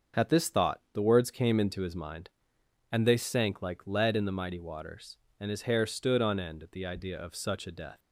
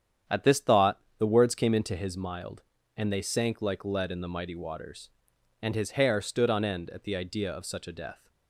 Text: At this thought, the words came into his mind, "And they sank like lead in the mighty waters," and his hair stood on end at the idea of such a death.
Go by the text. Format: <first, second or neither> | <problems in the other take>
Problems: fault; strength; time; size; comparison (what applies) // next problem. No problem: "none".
first | starts louder than the rest; strong; until 1.4 s; 9 dB; also in the first // says "mild" for "mind"; at 2.1 s